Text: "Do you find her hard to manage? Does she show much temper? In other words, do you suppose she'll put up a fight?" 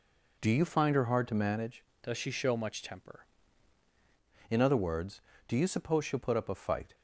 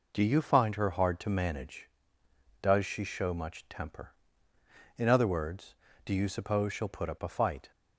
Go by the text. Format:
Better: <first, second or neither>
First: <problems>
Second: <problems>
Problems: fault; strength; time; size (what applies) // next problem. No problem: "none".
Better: second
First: changes voice from "Does" to "temper"; from 2.0 to 3.2 s; 1.2 s long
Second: none